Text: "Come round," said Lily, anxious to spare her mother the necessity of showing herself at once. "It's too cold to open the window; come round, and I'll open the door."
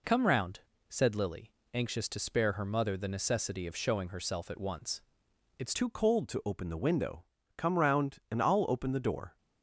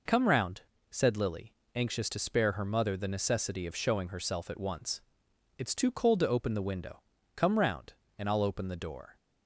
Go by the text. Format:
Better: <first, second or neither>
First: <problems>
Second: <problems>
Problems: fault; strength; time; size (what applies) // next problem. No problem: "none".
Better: second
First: changes voice at "too"; from 5.7 s on; 3.6 s long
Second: none